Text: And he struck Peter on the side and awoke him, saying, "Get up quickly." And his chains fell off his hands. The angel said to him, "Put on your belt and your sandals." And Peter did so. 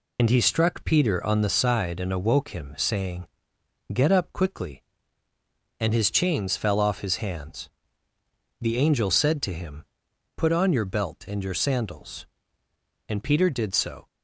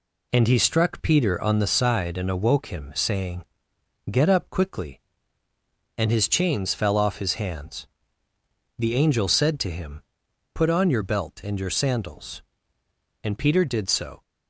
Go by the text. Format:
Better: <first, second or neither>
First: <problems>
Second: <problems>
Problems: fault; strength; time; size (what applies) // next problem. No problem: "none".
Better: second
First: loses the start of "And"; at 0.1 s; 55 ms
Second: none